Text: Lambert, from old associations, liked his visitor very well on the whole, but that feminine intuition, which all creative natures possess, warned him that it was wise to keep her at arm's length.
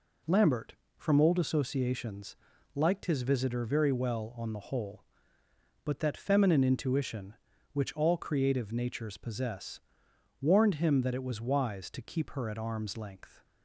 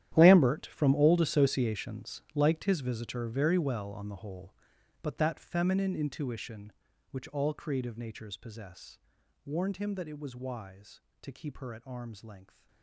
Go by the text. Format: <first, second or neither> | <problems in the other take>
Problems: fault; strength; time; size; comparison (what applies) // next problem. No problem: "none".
first | gets quieter; strong; throughout; 17 dB